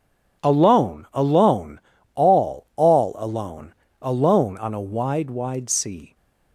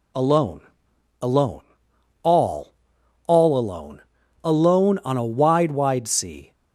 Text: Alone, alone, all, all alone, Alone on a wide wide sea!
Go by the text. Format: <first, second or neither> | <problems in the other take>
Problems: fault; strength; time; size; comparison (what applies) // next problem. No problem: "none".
neither | none